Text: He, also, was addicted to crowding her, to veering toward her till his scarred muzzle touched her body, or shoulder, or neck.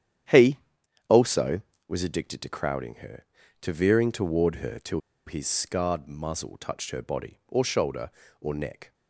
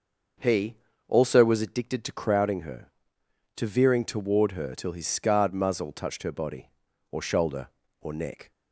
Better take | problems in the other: second | starts louder than the rest; strong; until 2.0 s; 10 dB // pauses between "till" and "his"; slight; at 4.9 s; 0.27 s long

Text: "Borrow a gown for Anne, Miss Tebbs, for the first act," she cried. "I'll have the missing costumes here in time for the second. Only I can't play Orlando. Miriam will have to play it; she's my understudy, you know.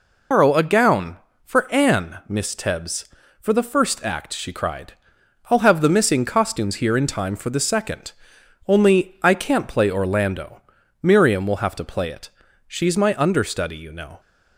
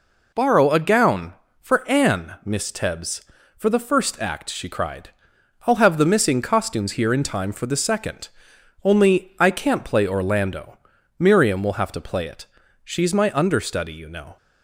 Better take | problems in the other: second | loses the start of "Borrow"; at 0.3 s; 125 ms

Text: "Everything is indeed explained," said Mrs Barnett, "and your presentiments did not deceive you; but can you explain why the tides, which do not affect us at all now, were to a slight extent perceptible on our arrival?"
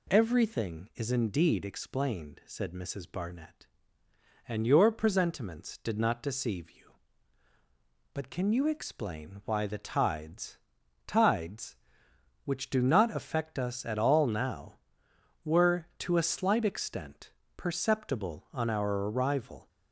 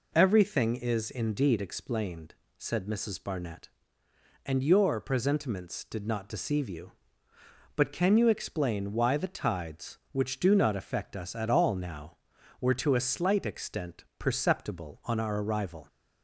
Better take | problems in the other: second | says "tides" twice; at 11.0 s // pauses between "extent" and "perceptible"; slight; at 17.3 s; 0.26 s long; slight in the second

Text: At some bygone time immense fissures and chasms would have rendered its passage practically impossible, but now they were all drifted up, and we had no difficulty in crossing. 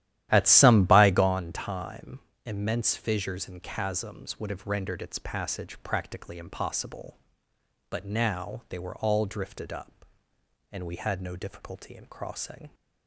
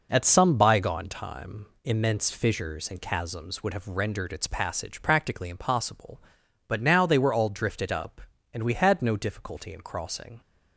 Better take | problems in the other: second | starts louder than the rest; strong; until 1.4 s; 12.5 dB // pauses between "time" and "immense"; slight; at 2.1 s; 0.26 s long; slight in the second

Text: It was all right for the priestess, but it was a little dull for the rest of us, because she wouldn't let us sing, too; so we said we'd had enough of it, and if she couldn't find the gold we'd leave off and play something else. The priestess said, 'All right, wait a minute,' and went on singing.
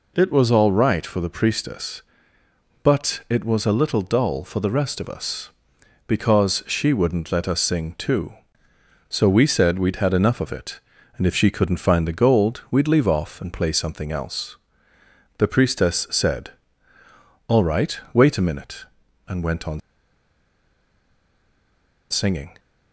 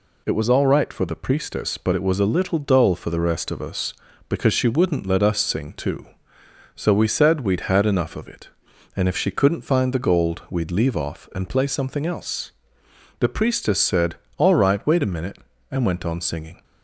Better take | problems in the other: second | pauses between "on" and "singing"; strong; at 19.8 s; 2.3 s long

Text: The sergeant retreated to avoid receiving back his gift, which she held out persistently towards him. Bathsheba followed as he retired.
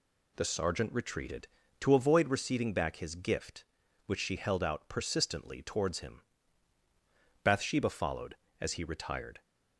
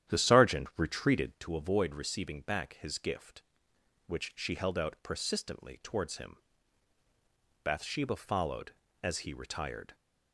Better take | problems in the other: first | starts louder than the rest; strong; until 1.4 s; 10.5 dB

